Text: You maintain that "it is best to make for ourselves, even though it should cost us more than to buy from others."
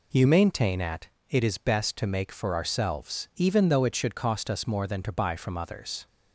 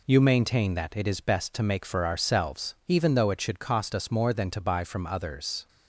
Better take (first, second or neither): second